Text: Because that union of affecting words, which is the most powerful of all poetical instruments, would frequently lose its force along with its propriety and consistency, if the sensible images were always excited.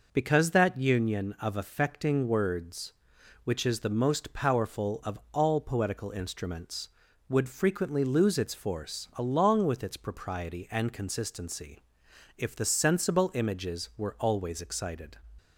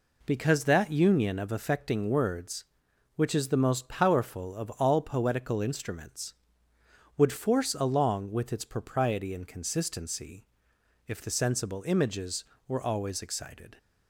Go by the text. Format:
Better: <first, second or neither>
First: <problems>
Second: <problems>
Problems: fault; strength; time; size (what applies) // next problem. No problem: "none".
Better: first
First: none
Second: skips "frequently lose its"; at 7.3 s